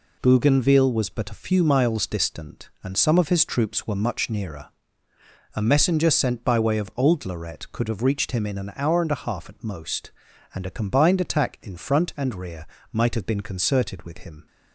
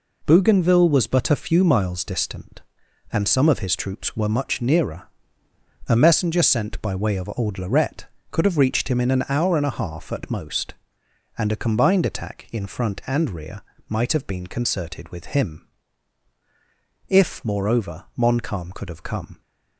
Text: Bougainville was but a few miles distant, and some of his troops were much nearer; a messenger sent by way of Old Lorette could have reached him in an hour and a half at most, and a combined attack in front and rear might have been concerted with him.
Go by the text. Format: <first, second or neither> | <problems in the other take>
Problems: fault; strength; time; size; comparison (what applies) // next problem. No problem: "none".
first | pauses between "rear" and "might"; slight; at 13.6 s; 0.26 s long; slight in the first // goes on to say "If moreover Montcalm could have come"; strong; from 17.0 s on; 2.3 s long